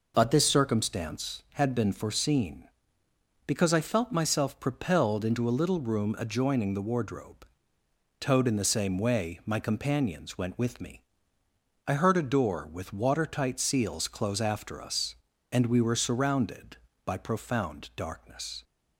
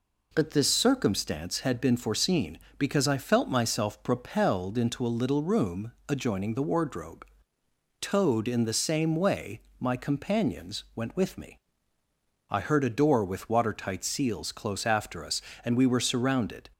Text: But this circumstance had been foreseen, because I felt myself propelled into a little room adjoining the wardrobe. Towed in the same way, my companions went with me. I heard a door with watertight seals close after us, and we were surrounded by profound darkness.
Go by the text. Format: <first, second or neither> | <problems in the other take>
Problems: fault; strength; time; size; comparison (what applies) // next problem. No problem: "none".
first | pauses between "room" and "adjoining"; slight; at 5.9 s; 0.16 s long // stops before "by profound darkness"; at 16.7 s